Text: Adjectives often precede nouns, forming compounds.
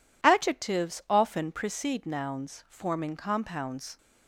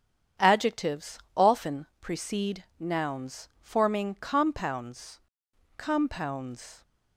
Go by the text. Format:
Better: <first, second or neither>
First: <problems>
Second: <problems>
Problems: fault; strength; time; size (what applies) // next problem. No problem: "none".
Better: first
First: none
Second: starts louder than the rest; strong; until 1.5 s; 9 dB // pauses between "Adjectives" and "often"; slight; at 1.2 s; 0.16 s long // pauses between "precede" and "nouns"; slight; at 2.6 s; 0.16 s long // says "compounds" twice; at 5.7 s